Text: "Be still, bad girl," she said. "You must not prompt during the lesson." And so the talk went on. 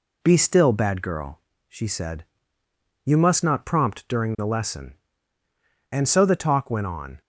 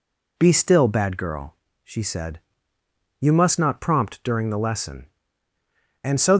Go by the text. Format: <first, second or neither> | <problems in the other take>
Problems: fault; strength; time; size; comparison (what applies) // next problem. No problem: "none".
first | stops before "the talk went on"; at 6.3 s